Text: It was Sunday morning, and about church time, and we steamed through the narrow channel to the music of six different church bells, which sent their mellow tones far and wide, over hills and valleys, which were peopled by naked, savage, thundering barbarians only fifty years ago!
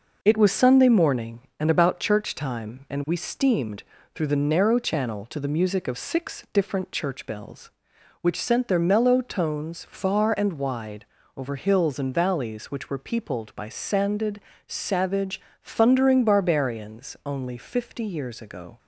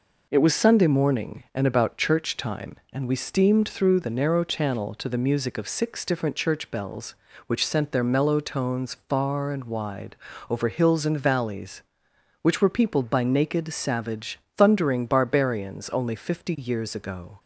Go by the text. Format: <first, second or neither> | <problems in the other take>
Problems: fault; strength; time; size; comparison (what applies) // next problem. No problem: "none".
second | pauses between "steamed" and "through"; slight; at 3.8 s; 0.32 s long // says "sanded" for "naked"; at 13.6 s